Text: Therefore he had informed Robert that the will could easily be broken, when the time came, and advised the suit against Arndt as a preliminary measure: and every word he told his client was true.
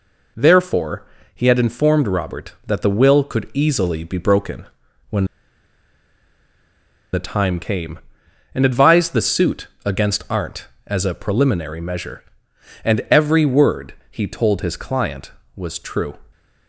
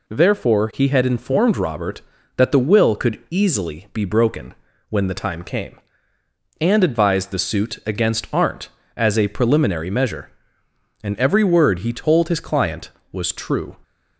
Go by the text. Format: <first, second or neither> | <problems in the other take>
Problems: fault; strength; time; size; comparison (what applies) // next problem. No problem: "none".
second | pauses between "Therefore" and "he"; slight; at 1.0 s; 0.28 s long // pauses between "when" and "the"; strong; at 5.2 s; 1.8 s long // pauses between "suit" and "against"; slight; at 9.6 s; 0.18 s long // pauses between "word" and "he"; slight; at 13.9 s; 0.16 s long